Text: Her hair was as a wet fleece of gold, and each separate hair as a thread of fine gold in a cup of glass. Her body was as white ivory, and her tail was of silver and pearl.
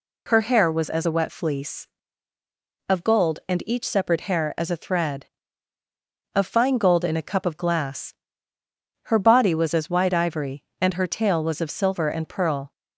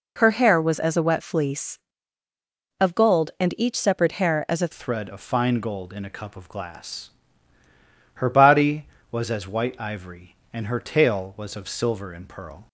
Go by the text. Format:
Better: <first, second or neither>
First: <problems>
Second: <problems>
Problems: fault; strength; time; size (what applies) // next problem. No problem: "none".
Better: first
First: none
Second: changes voice at "thread"; from 4.7 s on; 7.9 s long